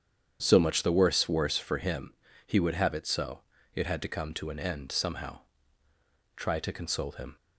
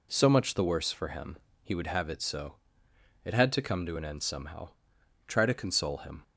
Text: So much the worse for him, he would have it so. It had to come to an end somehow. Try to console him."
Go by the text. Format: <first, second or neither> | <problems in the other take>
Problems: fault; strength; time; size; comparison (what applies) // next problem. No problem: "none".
second | starts louder than the rest; strong; until 1.4 s; 8.5 dB // says "worse" twice; at 1.2 s